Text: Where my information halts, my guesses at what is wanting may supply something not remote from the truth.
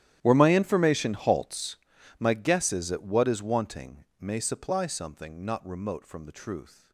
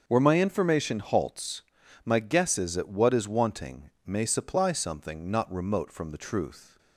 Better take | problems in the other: second | gets quieter; strong; throughout; 20.5 dB // starts louder than the rest; strong; until 1.2 s; 12 dB; also in the second // pauses between "wanting" and "may"; slight; at 4.0 s; 0.16 s long; slight in the second

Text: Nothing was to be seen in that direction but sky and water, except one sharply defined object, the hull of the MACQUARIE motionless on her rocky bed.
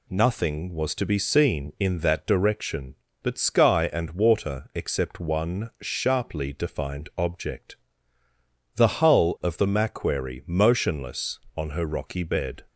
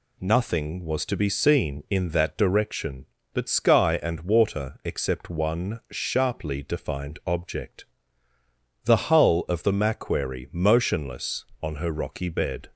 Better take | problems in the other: neither | none

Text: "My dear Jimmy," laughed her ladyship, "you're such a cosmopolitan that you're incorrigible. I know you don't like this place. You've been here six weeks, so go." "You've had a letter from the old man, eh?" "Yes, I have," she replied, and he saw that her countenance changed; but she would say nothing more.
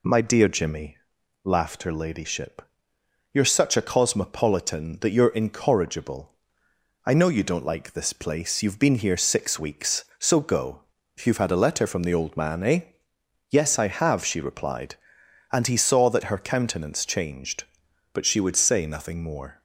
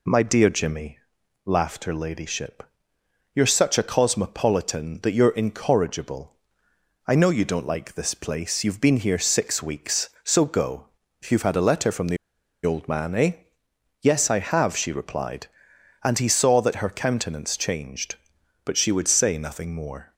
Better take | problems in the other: first | pauses between "the" and "old"; noticeable; at 12.1 s; 0.48 s long

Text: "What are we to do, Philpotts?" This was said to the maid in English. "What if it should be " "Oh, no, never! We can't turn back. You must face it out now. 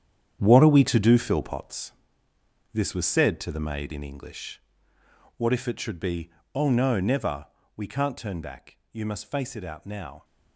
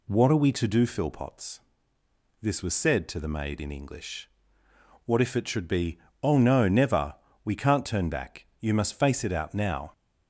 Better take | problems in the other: second | gets quieter; strong; throughout; 12 dB

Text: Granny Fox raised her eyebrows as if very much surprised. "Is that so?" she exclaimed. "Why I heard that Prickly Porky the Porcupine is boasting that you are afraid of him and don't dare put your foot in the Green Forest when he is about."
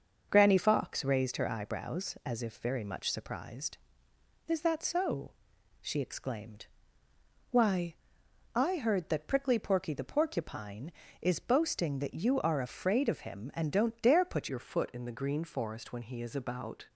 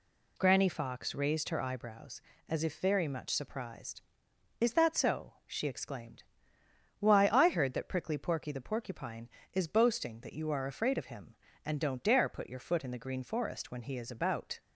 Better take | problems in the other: second | starts louder than the rest; until 1.3 s; 6 dB // pauses between "Why" and "I"; noticeable; at 7.9 s; 0.60 s long // changes voice at "your"; from 14.4 s on; 2.4 s long

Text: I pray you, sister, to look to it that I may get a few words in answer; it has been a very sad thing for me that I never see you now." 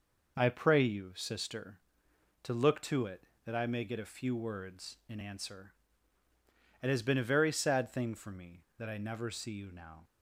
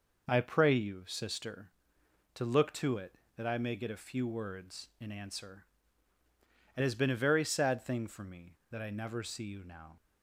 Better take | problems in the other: neither | none

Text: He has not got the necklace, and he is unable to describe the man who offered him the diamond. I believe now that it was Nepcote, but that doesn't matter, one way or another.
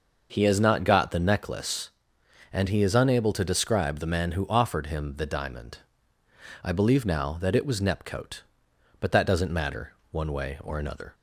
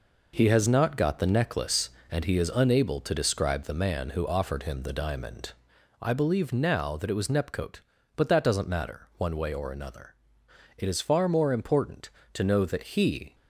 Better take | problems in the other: first | goes on to say "It is far more important to know that he"; strong; from 10.7 s on; 2.5 s long

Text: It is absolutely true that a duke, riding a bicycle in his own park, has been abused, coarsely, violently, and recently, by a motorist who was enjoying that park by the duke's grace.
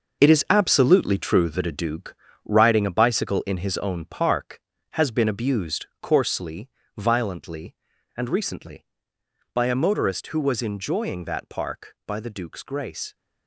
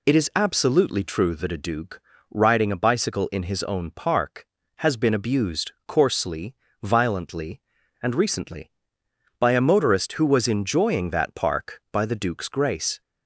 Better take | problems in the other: second | gets quieter; strong; throughout; 10 dB

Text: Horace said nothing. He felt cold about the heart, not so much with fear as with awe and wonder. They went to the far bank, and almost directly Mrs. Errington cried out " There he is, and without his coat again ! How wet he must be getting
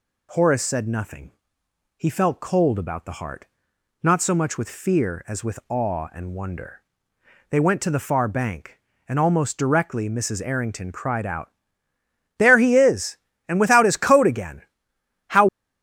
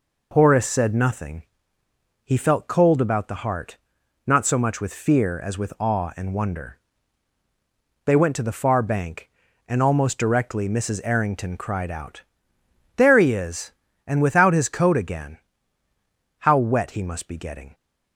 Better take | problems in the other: second | stops before "wet he must be getting"; at 15.4 s

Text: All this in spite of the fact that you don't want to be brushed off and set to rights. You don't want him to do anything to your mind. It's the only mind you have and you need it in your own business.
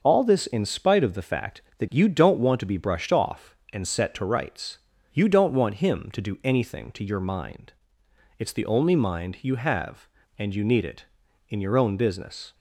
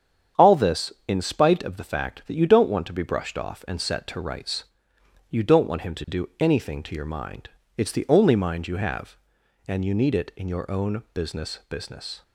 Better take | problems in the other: first | starts louder than the rest; strong; until 1.5 s; 8 dB; also in the first // says "business" twice; at 11.6 s

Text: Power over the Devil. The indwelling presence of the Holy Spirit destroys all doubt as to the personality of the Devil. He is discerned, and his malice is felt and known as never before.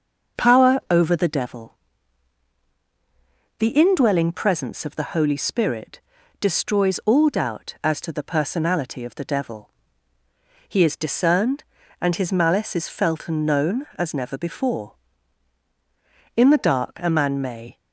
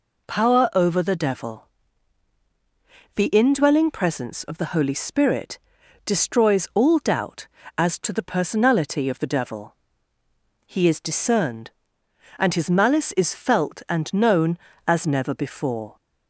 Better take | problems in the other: second | starts louder than the rest; until 1.4 s; 6.5 dB // pauses between "Spirit" and "destroys"; at 5.9 s; 0.42 s long; noticeable in the second // goes on to say "In the dark a man may"; from 16.3 s on; 1.4 s long

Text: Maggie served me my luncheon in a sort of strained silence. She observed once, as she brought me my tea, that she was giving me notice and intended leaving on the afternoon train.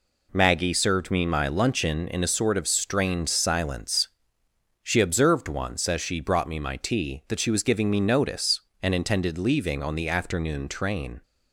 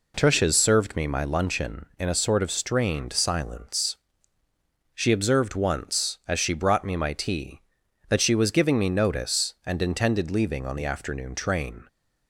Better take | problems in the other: first | says "Tushes" for "Maggie"; at 0.1 s

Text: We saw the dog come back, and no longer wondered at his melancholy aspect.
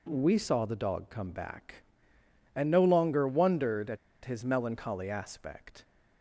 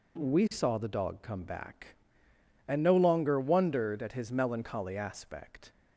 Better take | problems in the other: second | pauses between "at" and "his"; slight; at 3.9 s; 0.27 s long

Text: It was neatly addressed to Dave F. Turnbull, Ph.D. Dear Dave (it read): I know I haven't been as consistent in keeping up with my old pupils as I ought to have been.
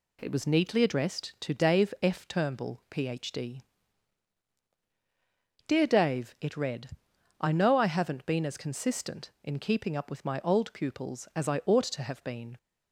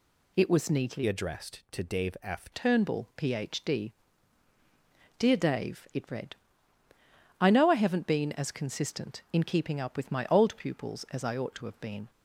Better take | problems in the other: first | changes voice from "addressed" to "F"; from 1.0 to 2.4 s; 1.4 s long

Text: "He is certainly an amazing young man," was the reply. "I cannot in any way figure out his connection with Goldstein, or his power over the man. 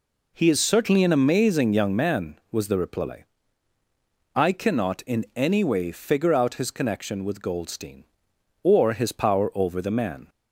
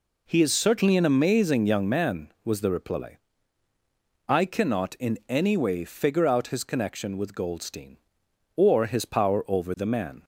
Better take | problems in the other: neither | none

